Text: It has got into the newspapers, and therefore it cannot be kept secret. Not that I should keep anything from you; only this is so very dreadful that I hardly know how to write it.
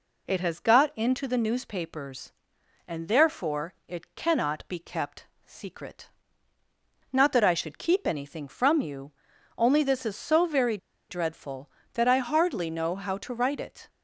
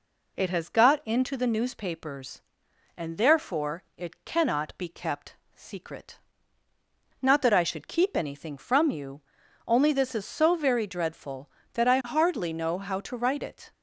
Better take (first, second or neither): second